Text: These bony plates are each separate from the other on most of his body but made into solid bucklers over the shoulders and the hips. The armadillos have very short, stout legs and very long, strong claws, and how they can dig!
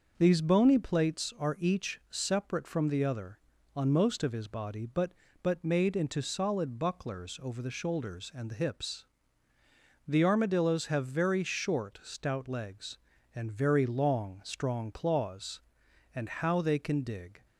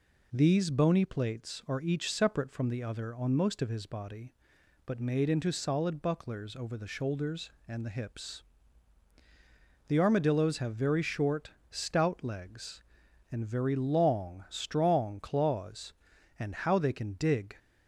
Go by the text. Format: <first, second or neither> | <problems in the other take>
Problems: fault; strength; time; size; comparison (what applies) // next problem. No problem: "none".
second | starts louder than the rest; noticeable; until 1.1 s; 6 dB // says "but" twice; at 5.4 s